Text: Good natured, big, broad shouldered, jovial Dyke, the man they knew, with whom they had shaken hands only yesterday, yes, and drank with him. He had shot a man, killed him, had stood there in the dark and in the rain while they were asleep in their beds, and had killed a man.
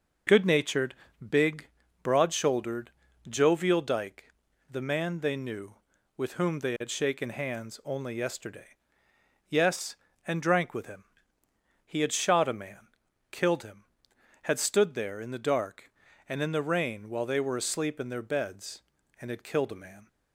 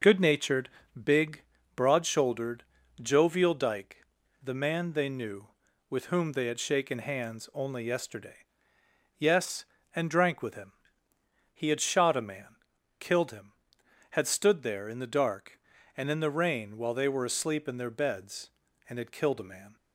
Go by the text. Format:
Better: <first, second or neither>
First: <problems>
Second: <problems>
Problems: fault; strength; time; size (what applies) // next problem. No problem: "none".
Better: neither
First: none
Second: none